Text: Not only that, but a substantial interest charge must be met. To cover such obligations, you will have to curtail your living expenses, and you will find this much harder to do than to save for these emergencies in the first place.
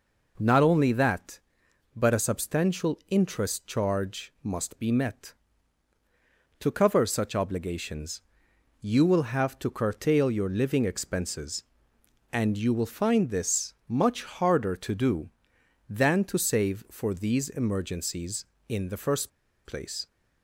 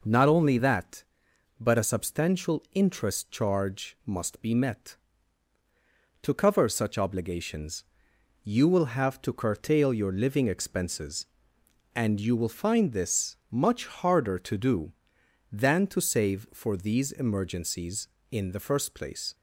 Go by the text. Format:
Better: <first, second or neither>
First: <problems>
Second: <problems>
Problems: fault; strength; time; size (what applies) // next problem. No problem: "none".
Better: second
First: pauses between "this" and "much"; slight; at 13.7 s; 0.16 s long // pauses between "first" and "place"; slight; at 19.3 s; 0.34 s long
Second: pauses between "this" and "much"; slight; at 13.3 s; 0.16 s long